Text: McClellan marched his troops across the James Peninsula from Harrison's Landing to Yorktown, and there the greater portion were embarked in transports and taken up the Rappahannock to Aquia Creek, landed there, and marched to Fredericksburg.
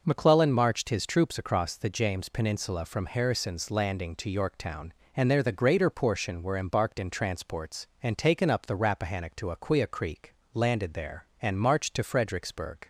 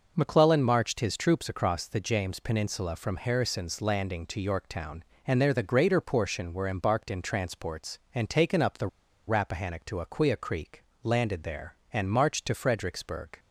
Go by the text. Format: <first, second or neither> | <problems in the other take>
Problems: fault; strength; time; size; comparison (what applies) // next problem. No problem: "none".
first | pauses between "the" and "Rappahannock"; at 8.8 s; 0.40 s long